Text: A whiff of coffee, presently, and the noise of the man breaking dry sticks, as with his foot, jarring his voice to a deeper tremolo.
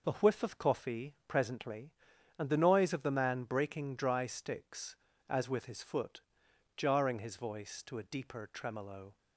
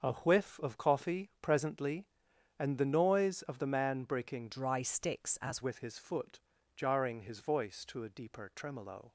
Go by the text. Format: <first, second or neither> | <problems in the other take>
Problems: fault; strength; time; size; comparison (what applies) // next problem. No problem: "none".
first | starts louder than the rest; until 1.0 s; 6.5 dB // changes voice from "dry" to "as"; from 4.5 to 5.6 s; 1.1 s long